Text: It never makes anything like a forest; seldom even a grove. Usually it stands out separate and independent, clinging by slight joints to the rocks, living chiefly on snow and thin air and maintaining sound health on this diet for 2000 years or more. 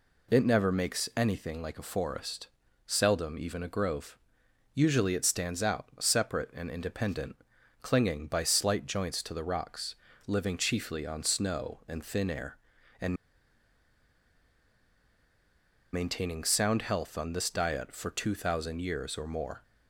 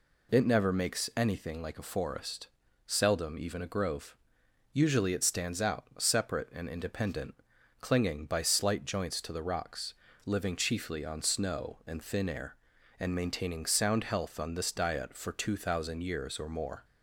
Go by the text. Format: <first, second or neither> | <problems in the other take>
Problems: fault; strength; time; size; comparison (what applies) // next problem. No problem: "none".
second | pauses between "and" and "maintaining"; strong; at 13.1 s; 2.7 s long